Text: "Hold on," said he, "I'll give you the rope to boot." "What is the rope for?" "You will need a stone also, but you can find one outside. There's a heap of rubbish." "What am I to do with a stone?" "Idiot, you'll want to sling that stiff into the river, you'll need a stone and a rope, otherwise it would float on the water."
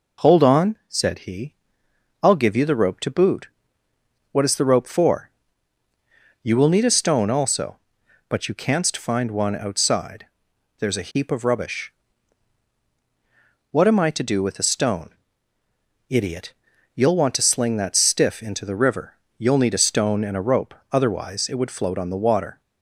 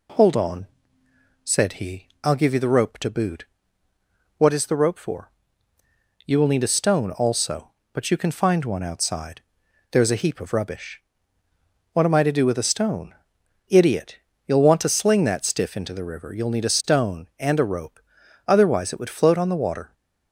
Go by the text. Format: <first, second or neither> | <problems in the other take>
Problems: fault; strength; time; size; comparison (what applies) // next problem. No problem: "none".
second | says "canst" for "can"; at 8.5 s